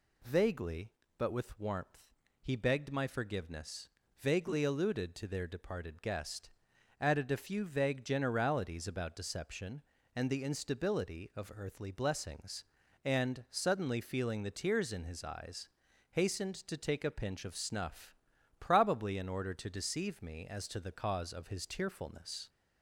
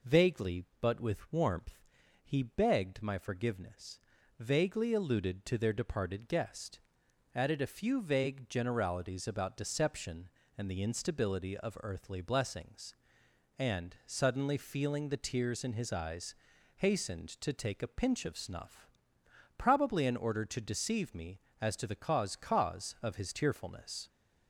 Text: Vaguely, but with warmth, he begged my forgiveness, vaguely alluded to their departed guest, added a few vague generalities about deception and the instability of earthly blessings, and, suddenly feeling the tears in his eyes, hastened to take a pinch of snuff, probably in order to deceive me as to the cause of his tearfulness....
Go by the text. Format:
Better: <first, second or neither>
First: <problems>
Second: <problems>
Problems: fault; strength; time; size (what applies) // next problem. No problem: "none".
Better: first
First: none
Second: says "cause" twice; at 22.3 s